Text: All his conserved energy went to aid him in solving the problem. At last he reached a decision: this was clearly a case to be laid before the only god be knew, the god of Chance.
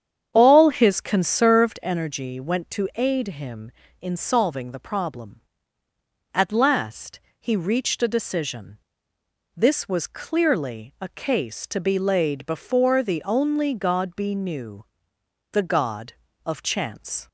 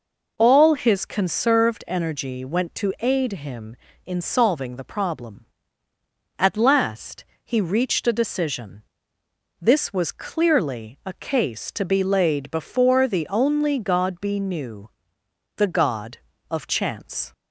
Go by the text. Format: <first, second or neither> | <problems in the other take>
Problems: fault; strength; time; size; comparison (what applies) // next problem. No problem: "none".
second | starts louder than the rest; strong; until 2.0 s; 8.5 dB // pauses between "last" and "he"; slight; at 7.1 s; 0.18 s long; slight in the second